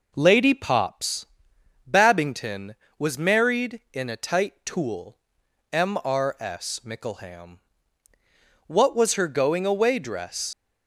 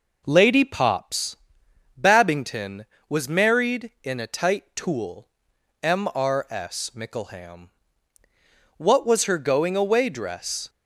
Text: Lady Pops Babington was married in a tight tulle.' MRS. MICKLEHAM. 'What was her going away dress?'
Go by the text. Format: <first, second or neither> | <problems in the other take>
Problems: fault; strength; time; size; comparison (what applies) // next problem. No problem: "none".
second | pauses between "Pops" and "Babington"; noticeable; at 1.2 s; 0.62 s long; noticeable in the second // leaves "dress" unfinished; at 10.5 s; 55 ms